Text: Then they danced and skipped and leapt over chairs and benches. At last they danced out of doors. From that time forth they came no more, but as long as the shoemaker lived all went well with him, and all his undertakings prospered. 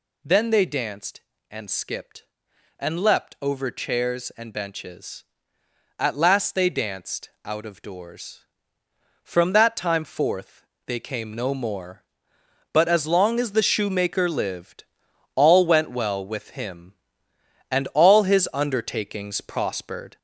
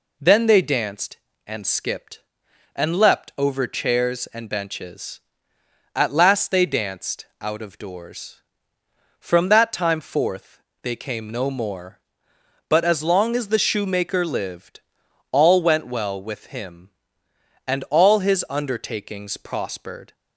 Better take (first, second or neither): second